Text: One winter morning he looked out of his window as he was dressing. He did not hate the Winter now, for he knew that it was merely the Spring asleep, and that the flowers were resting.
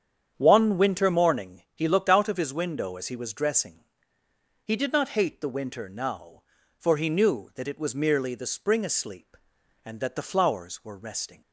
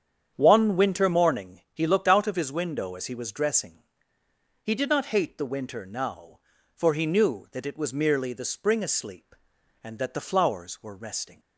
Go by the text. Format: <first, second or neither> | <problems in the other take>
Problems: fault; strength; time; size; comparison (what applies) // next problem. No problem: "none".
neither | starts louder than the rest; strong; the same in both